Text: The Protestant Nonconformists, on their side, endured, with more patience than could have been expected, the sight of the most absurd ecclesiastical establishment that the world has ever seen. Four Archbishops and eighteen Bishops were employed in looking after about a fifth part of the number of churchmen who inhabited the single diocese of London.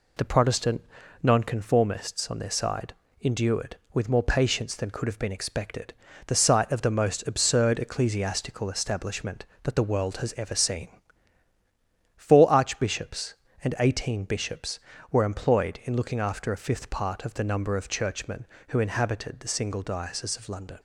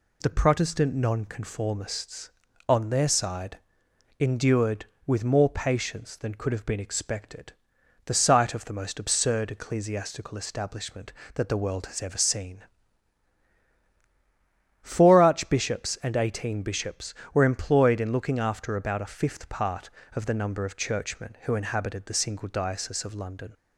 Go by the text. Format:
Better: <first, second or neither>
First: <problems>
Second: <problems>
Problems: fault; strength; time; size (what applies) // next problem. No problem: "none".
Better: second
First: pauses between "Protestant" and "Nonconformists"; at 0.8 s; 0.38 s long // skips "about"; at 16.5 s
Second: none